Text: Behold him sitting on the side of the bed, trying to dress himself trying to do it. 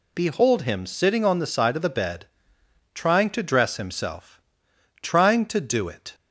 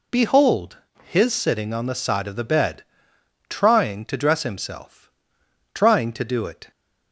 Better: first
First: pauses between "himself" and "trying"; noticeable; at 4.4 s; 0.62 s long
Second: says "his" for "him"; at 1.0 s // pauses between "himself" and "trying"; noticeable; at 4.9 s; 0.76 s long

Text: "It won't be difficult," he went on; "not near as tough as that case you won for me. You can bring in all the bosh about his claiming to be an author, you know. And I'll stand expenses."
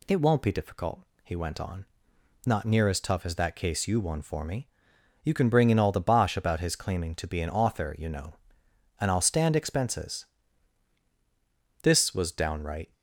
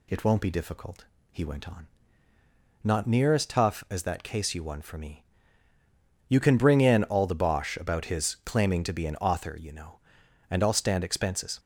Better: second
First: goes on to say "This was downright"; noticeable; from 11.8 s on; 1.1 s long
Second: none

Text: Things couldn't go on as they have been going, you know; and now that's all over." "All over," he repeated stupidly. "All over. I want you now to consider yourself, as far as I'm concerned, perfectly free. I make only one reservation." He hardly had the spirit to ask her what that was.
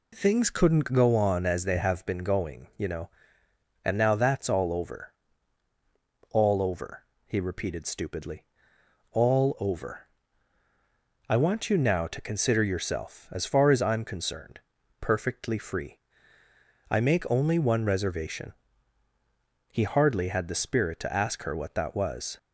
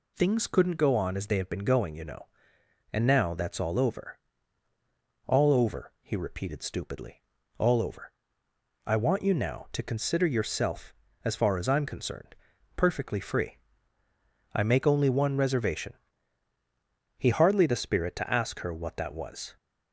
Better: first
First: none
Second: skips "had"; at 17.6 s

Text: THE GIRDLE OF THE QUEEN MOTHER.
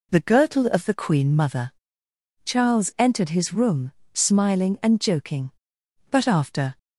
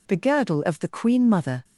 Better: second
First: goes on to say "Charles entered his room smiling and joking But after"; strong; from 2.4 s on; 4.3 s long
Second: none

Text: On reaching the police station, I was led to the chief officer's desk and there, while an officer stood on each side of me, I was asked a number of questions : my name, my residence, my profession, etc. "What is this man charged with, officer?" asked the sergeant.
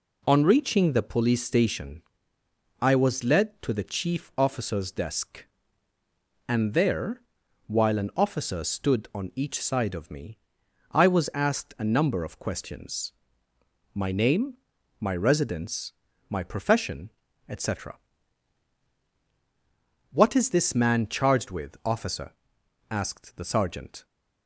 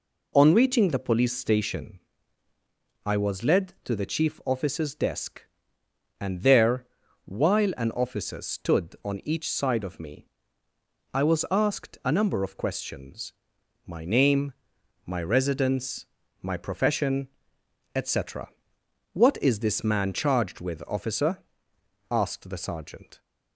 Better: neither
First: none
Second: none

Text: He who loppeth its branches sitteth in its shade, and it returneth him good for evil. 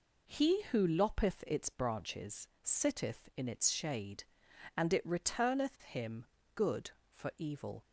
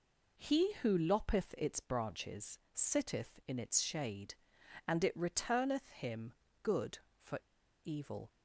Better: first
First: pauses between "branches" and "sitteth"; slight; at 2.4 s; 0.16 s long // pauses between "him" and "good"; slight; at 6.2 s; 0.28 s long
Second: pauses between "branches" and "sitteth"; slight; at 2.5 s; 0.16 s long // pauses between "him" and "good"; slight; at 6.3 s; 0.28 s long // pauses between "for" and "evil"; noticeable; at 7.3 s; 0.46 s long

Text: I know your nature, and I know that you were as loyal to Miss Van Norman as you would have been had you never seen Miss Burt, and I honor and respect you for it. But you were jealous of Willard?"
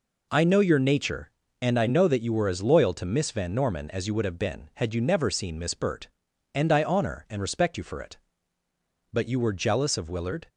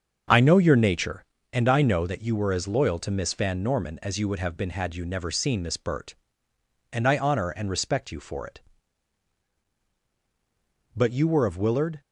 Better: first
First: none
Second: starts louder than the rest; until 1.5 s; 6.5 dB // skips "jealous"; at 11.4 s

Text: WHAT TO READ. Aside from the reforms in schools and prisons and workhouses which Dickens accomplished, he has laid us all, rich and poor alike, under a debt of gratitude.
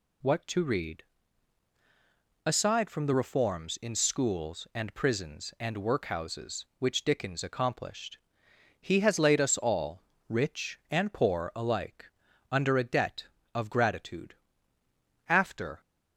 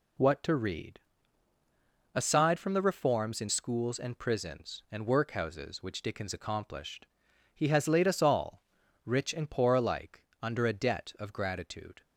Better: second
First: goes on to say "After"; from 15.2 s on; 0.52 s long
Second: none

